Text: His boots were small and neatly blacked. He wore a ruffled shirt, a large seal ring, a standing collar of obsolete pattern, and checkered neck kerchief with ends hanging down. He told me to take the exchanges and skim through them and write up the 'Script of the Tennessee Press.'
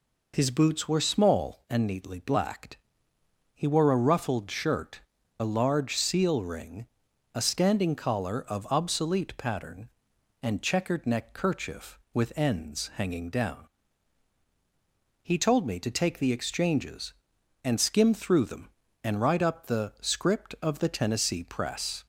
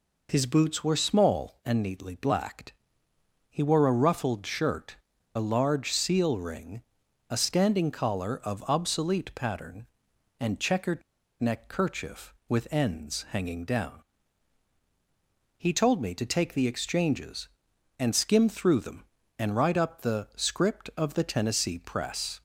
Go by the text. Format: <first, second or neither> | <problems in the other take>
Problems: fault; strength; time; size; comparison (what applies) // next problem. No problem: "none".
first | pauses between "checkered" and "neck"; at 11.0 s; 0.37 s long